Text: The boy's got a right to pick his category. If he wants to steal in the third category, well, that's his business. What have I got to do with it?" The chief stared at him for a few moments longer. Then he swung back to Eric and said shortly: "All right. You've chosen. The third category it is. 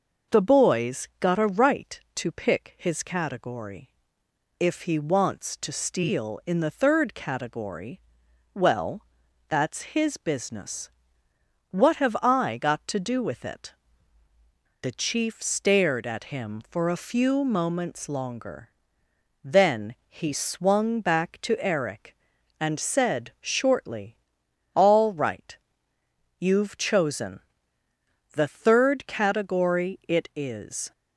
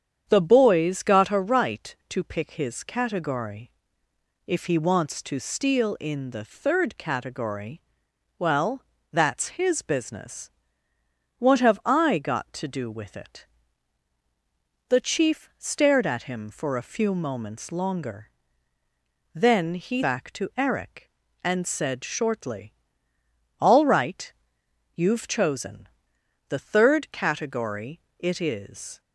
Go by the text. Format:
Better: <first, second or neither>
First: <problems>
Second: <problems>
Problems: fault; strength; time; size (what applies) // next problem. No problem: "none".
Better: first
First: none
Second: starts louder than the rest; strong; until 1.2 s; 8 dB // skips "swung"; at 20.0 s // pauses between "category" and "it"; slight; at 28.0 s; 0.18 s long